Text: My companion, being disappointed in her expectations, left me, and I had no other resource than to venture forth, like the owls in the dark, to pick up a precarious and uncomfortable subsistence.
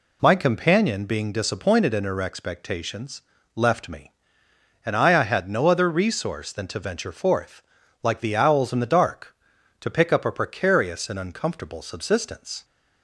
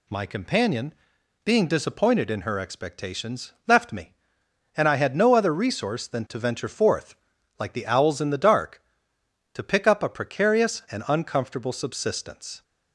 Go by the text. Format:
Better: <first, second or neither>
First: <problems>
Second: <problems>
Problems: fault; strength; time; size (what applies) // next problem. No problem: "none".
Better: second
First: says "I" twice; at 5.1 s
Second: none